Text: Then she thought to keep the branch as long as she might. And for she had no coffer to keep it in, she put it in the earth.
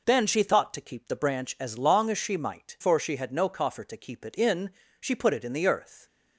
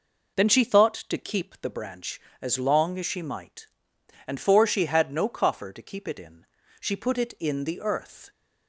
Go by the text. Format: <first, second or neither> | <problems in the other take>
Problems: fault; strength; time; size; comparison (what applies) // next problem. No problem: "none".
second | skips "And"; at 2.7 s